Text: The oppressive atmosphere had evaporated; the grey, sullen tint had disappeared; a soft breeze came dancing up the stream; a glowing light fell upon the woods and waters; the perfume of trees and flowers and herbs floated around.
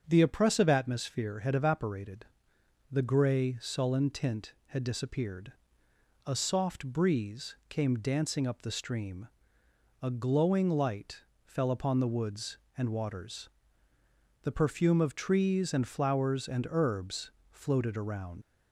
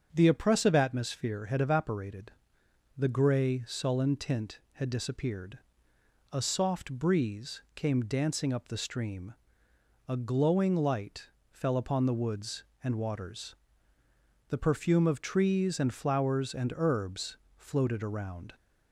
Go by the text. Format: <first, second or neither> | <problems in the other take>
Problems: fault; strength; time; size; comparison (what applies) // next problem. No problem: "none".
second | starts louder than the rest; until 1.0 s; 7 dB; also in the second // pauses between "light" and "fell"; slight; at 11.2 s; 0.24 s long; slight in the second // pauses between "herbs" and "floated"; slight; at 17.2 s; 0.20 s long; slight in the second // leaves "around" unfinished; at 18.4 s; 70 ms